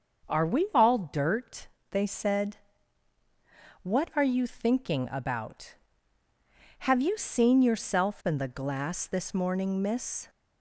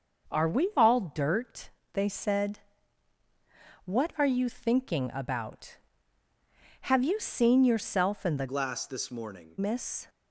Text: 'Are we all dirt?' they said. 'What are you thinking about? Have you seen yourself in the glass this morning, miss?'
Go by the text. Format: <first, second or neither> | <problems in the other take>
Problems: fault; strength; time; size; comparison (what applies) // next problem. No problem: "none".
first | starts louder than the rest; noticeable; until 1.3 s; 6 dB; also in the first // changes voice from "glass" to "morning"; from 8.4 to 9.5 s; 1.1 s long